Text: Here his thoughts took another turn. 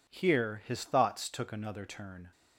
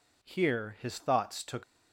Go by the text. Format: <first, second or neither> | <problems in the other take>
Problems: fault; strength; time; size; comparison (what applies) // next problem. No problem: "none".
first | stops before "another turn"; at 1.6 s